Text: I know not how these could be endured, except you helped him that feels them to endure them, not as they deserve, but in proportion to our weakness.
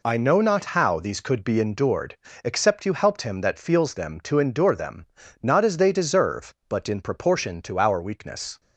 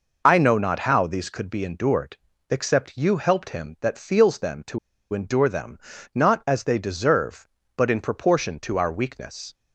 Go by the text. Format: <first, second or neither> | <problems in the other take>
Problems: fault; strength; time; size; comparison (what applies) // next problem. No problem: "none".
first | pauses between "to" and "endure"; slight; at 4.7 s; 0.35 s long